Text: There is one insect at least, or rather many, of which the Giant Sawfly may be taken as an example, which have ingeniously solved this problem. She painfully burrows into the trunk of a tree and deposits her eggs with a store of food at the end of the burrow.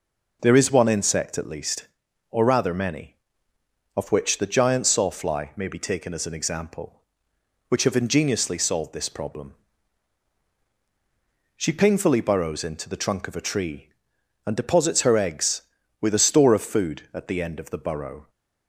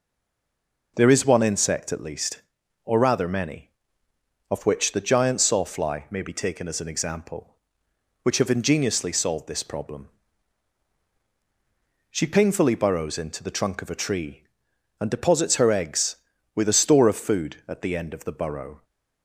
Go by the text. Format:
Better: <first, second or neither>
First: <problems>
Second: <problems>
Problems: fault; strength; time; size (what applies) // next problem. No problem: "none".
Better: first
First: none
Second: stays silent before the first word; slight; until 0.9 s; 0.9 s long